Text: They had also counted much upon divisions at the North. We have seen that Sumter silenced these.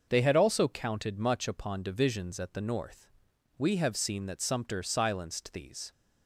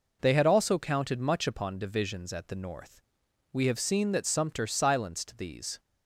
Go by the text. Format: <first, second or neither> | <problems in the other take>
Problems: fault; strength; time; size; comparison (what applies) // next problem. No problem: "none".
neither | none